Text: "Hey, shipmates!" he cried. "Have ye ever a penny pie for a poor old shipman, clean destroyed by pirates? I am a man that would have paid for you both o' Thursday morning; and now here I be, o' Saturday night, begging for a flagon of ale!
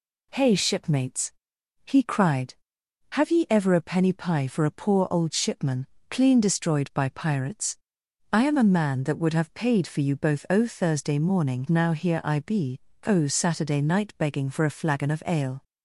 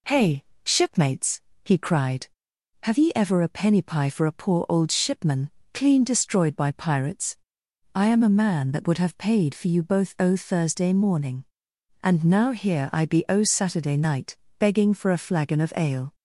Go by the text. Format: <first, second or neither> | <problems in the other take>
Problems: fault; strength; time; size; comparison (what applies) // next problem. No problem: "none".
second | skips "and"; at 11.6 s